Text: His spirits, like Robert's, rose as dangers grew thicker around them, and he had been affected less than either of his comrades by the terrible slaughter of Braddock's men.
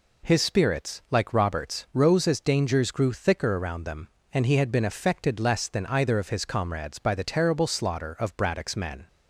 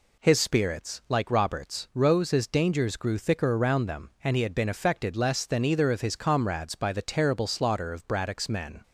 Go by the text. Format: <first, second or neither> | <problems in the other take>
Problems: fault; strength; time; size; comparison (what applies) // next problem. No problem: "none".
neither | none